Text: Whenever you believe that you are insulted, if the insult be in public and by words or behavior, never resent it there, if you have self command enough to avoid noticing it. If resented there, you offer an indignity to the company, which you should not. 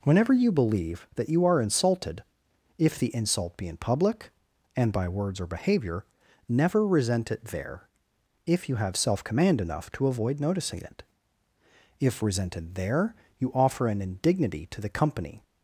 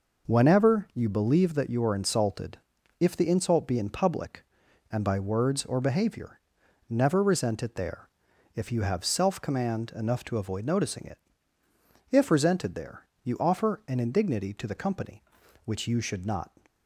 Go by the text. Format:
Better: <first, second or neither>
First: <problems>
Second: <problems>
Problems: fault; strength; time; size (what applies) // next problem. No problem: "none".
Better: second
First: stops before "which you should not"; at 15.4 s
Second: none